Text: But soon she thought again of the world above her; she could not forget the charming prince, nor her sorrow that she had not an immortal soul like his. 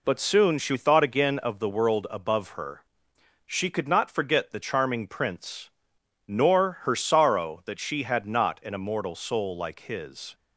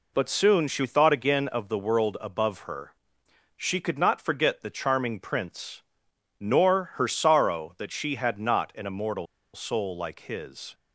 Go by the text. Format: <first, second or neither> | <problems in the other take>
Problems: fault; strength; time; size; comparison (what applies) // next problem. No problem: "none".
first | pauses between "immortal" and "soul"; slight; at 9.2 s; 0.28 s long